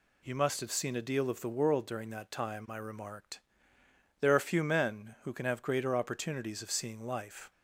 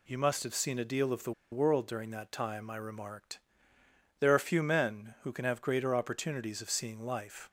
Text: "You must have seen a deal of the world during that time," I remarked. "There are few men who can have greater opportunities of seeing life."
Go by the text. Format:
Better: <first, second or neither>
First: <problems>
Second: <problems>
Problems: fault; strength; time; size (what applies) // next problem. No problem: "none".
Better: first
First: none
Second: pauses between "the" and "world"; slight; at 1.3 s; 0.20 s long